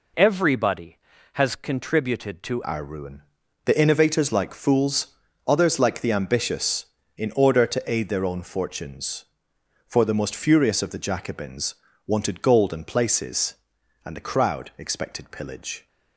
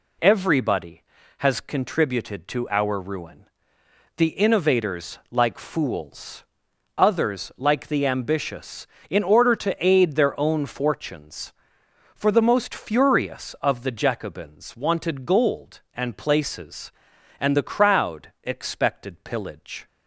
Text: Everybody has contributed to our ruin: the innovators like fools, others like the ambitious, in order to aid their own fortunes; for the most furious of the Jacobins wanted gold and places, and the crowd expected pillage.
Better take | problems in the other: second | changes voice at "our"; from 2.6 s on; 13.2 s long // pauses between "Jacobins" and "wanted"; slight; at 11.7 s; 0.30 s long

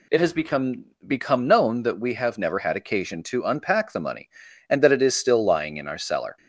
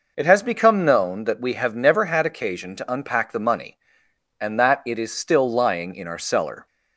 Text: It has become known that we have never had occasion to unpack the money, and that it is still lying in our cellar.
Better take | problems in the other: second | says "become" twice; at 1.0 s

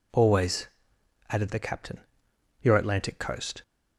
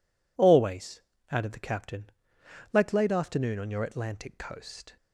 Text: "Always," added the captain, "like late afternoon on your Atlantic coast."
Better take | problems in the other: second | skips "like late afternoon on"; at 2.3 s

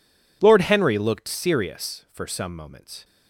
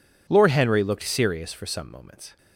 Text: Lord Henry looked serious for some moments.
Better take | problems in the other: neither | none

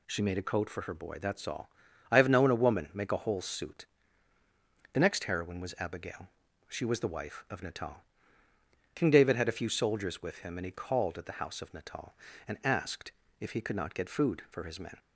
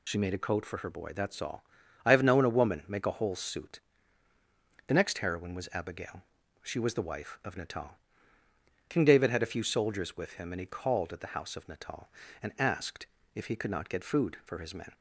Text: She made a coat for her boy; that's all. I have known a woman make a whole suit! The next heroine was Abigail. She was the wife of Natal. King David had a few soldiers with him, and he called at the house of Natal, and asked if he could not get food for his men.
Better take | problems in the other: first | loses the start of "She"; at 0.0 s; 50 ms // pauses between "asked" and "if"; slight; at 13.0 s; 0.28 s long; slight in the first

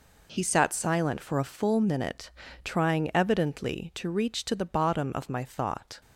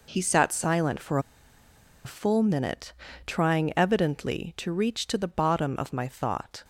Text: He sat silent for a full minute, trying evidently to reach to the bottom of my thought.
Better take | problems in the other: first | pauses between "for" and "a"; noticeable; at 1.1 s; 0.86 s long

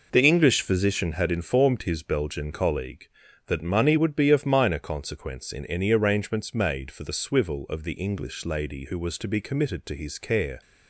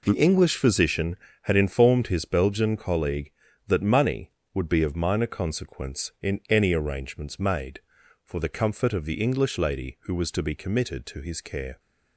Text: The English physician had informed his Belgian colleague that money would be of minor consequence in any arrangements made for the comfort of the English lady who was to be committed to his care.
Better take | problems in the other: second | says "swivel" for "comfort"; at 7.1 s

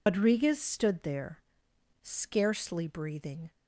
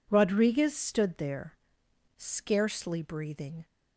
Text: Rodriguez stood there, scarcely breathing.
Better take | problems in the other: second | loses the start of "Rodriguez"; at 0.0 s; 130 ms

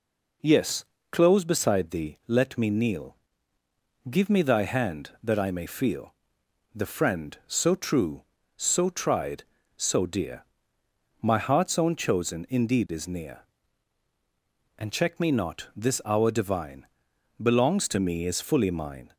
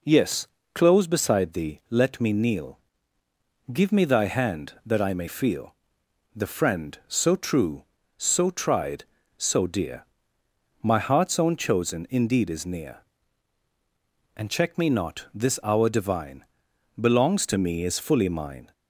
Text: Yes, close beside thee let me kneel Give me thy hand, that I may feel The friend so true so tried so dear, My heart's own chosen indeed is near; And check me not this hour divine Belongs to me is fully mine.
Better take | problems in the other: neither | pauses between "kneel" and "Give"; noticeable; the same in both // pauses between "feel" and "The"; noticeable; the same in both // pauses between "divine" and "Belongs"; noticeable; the same in both

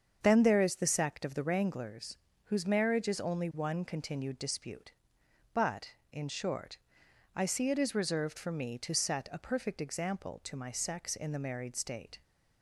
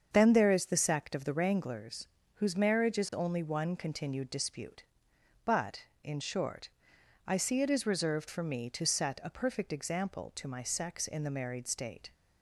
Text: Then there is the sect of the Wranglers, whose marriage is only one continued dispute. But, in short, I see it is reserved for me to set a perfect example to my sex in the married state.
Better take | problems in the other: neither | starts louder than the rest; strong; the same in both

